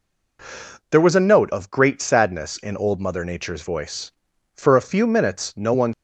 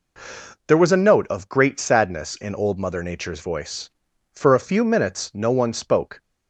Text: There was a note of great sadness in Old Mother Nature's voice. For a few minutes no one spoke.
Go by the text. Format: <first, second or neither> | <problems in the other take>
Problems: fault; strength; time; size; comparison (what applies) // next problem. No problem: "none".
second | stops before "spoke"; at 5.9 s